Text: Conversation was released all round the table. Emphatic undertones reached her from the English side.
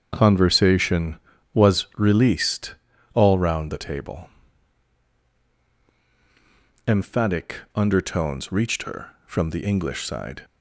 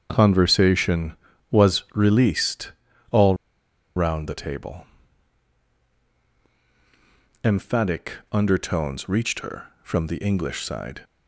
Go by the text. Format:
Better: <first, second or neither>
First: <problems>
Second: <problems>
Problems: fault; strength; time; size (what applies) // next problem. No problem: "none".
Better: first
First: starts louder than the rest; strong; until 1.1 s; 7.5 dB // pauses between "released" and "all"; at 2.7 s; 0.38 s long // pauses between "Emphatic" and "undertones"; slight; at 7.5 s; 0.18 s long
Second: starts louder than the rest; strong; until 1.1 s; 7.5 dB // pauses between "released" and "all"; at 2.7 s; 0.38 s long // pauses between "all" and "round"; noticeable; at 3.3 s; 0.61 s long // pauses between "Emphatic" and "undertones"; slight; at 8.1 s; 0.18 s long